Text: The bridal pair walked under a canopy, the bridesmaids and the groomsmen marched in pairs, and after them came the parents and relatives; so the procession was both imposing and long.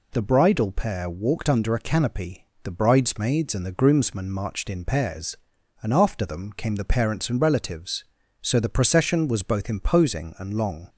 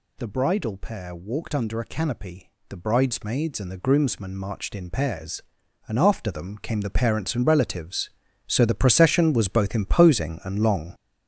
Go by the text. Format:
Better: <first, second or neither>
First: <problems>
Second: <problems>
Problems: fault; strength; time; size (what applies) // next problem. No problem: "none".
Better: first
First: none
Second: gets louder; strong; throughout; 8 dB